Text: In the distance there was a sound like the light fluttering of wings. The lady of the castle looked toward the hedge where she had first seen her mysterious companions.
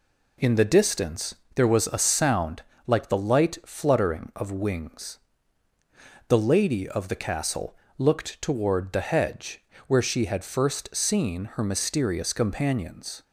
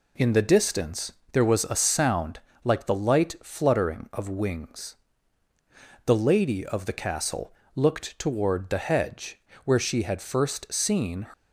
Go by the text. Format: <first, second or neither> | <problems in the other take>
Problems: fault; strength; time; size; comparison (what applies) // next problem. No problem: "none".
first | pauses between "distance" and "there"; slight; at 1.1 s; 0.20 s long; slight in the first // pauses between "sound" and "like"; slight; at 2.3 s; 0.26 s long; slight in the first // pauses between "castle" and "looked"; slight; at 7.5 s; 0.22 s long; slight in the first // pauses between "hedge" and "where"; slight; at 9.3 s; 0.26 s long; slight in the first // stops before "her mysterious companions"; at 11.3 s